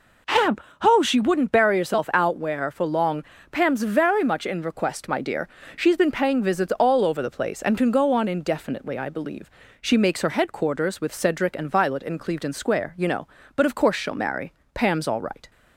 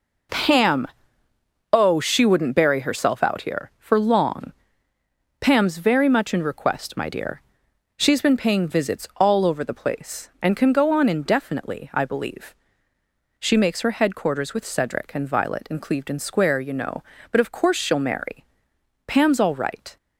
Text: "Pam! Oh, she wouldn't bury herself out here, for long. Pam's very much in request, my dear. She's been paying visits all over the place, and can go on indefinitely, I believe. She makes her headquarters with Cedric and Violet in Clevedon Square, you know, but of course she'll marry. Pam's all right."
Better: second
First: says "where" for "here"; at 2.3 s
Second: none

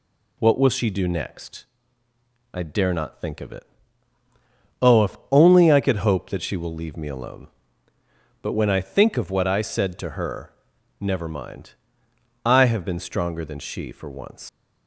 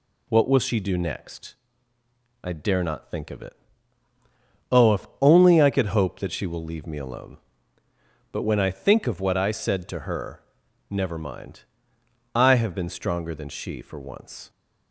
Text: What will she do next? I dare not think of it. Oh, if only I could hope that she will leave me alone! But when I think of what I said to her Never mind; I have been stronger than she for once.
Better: second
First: pauses between "her" and "Never"; noticeable; at 10.5 s; 0.48 s long // leaves "once" unfinished; at 14.4 s; 105 ms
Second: pauses between "her" and "Never"; noticeable; at 10.4 s; 0.48 s long

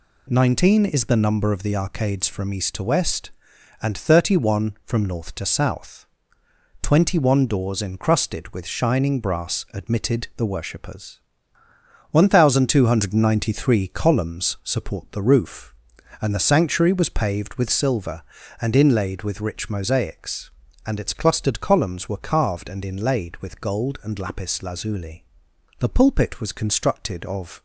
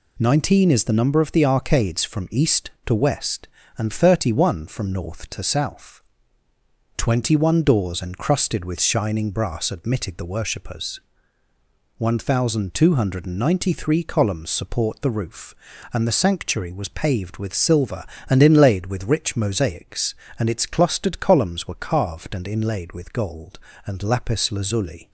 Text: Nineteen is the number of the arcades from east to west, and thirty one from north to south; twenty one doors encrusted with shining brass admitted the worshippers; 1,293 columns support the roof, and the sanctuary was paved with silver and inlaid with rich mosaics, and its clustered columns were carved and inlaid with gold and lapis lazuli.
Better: second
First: goes on to say "The pulpit was constructed of"; strong; from 25.7 s on; 1.8 s long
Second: none

